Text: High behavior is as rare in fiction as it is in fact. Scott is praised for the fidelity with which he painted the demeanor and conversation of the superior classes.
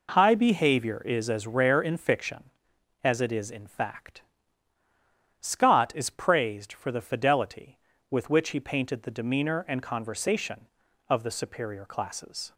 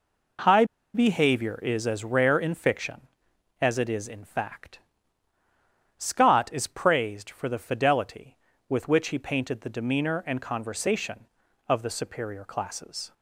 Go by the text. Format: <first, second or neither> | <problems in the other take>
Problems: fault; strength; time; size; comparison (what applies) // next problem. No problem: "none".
first | pauses between "High" and "behavior"; slight; at 0.6 s; 0.30 s long